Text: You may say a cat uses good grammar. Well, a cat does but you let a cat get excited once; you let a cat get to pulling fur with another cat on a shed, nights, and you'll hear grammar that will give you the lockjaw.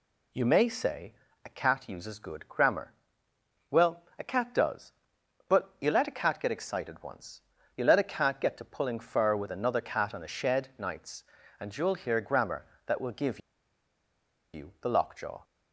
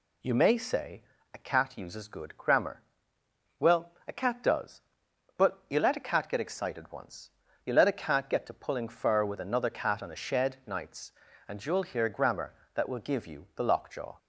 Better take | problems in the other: second | pauses between "say" and "a"; slight; at 1.1 s; 0.32 s long; slight in the second // pauses between "give" and "you"; at 13.3 s; 1.1 s long

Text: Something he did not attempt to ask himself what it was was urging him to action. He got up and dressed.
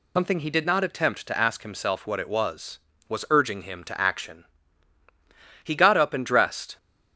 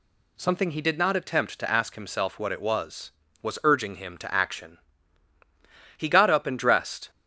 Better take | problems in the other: second | loses the start of "Something"; at 0.1 s; 100 ms

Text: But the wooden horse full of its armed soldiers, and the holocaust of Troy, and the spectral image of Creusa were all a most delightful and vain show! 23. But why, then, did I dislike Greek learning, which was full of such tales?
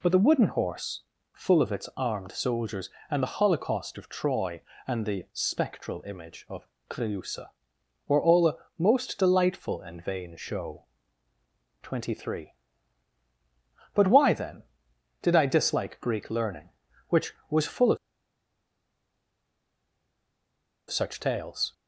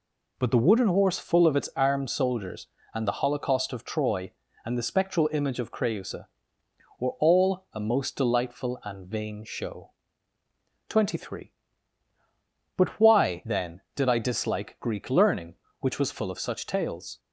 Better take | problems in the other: second | pauses between "horse" and "full"; slight; at 1.0 s; 0.30 s long // pauses between "of" and "Creusa"; slight; at 6.6 s; 0.22 s long // pauses between "a" and "most"; slight; at 8.5 s; 0.20 s long // pauses between "of" and "such"; strong; at 17.9 s; 2.9 s long

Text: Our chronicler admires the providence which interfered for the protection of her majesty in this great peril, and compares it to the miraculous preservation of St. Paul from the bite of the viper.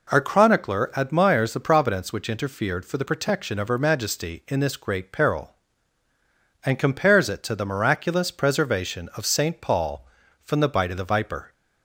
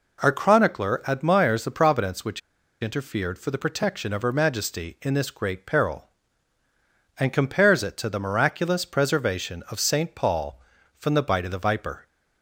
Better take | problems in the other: first | pauses between "which" and "interfered"; at 2.4 s; 0.42 s long

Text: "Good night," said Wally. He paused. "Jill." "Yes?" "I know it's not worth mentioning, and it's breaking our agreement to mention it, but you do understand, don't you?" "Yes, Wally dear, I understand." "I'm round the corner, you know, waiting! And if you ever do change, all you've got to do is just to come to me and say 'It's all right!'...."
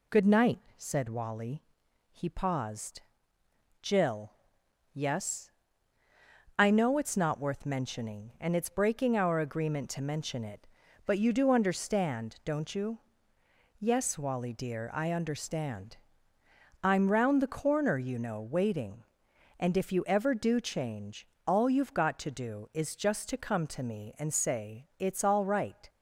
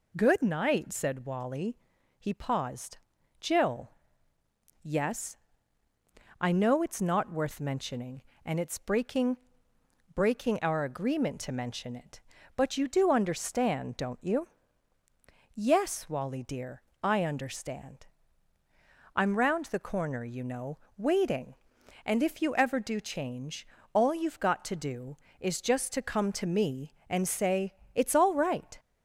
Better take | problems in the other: first | says "breaking" twice; at 10.1 s // pauses between "say" and "It's"; slight; at 27.7 s; 0.22 s long

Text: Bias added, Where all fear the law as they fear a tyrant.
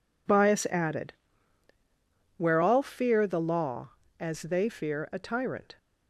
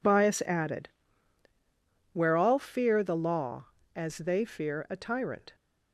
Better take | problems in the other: neither | none

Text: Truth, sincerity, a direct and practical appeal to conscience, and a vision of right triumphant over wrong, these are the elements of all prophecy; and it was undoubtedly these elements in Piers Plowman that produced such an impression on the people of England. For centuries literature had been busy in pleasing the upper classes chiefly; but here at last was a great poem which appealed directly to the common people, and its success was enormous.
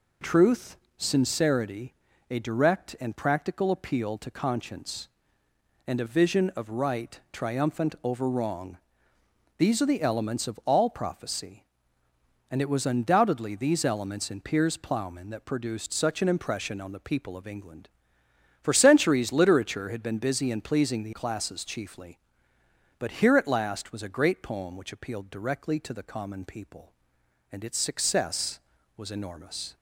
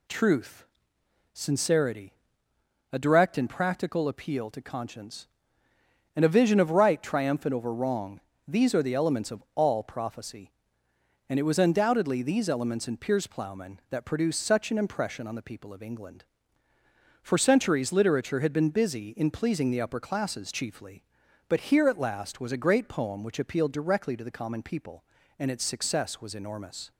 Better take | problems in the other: second | skips "upper"; at 21.1 s

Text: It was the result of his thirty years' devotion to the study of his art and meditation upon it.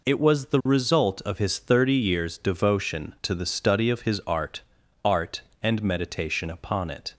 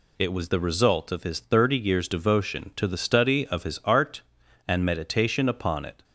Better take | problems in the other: second | says "art" twice; at 5.0 s

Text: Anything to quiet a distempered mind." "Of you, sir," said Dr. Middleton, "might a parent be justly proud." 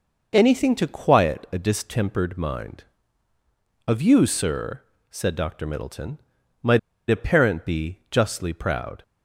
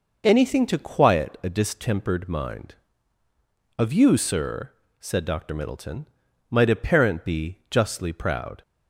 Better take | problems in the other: second | pauses between "might" and "a"; slight; at 6.7 s; 0.30 s long

